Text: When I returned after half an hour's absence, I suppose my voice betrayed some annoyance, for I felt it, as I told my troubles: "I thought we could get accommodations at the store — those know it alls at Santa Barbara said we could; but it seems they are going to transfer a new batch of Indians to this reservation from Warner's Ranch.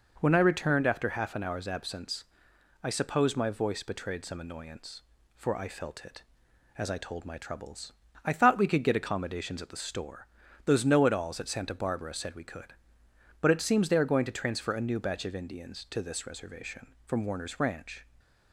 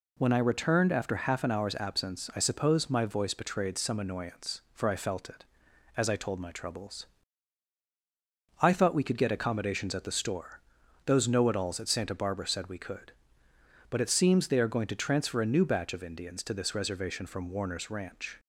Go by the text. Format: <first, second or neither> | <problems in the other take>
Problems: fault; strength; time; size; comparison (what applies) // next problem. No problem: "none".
neither | none